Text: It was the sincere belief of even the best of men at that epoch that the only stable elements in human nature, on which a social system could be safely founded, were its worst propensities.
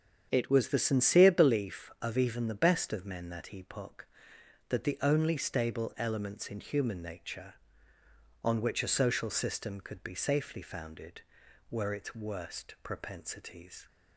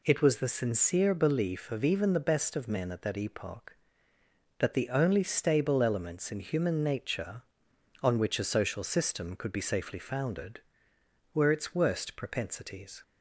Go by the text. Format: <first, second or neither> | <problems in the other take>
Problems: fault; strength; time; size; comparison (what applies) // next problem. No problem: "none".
second | starts louder than the rest; strong; until 1.3 s; 8 dB // skips "at"; at 3.2 s